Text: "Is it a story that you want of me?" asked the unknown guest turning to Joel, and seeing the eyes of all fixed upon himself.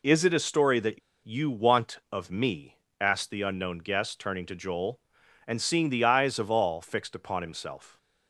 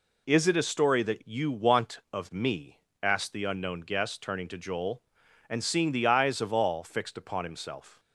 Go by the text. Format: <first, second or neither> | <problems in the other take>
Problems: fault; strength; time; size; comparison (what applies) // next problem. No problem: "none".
second | pauses between "that" and "you"; slight; at 1.0 s; 0.25 s long